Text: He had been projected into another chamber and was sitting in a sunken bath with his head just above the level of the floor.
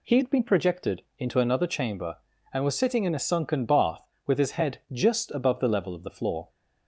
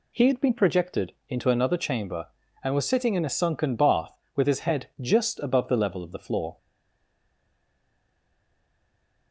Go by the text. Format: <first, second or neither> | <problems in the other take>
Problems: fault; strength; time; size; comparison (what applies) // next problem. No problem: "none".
first | stays silent after the last word; strong; from 6.5 s on; 2.8 s long